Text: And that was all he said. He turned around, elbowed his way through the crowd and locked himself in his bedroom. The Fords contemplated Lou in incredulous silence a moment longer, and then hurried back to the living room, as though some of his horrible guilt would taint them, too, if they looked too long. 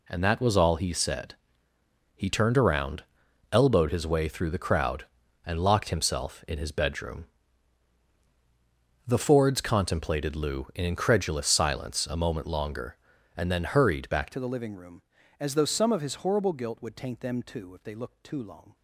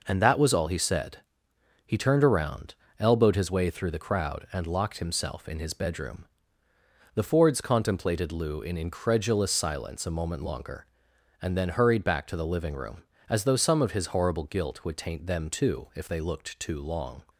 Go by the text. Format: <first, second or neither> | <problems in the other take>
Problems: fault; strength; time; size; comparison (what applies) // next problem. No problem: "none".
second | changes voice at "to"; from 14.3 s on; 4.4 s long